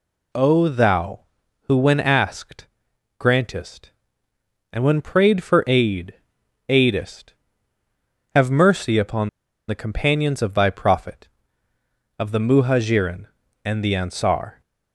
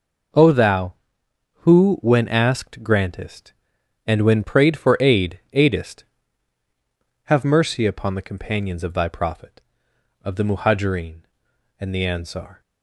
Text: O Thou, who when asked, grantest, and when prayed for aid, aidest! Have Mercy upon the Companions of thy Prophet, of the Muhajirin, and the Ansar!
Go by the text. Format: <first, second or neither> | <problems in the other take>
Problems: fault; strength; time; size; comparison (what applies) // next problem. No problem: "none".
second | pauses between "upon" and "the"; at 9.2 s; 0.39 s long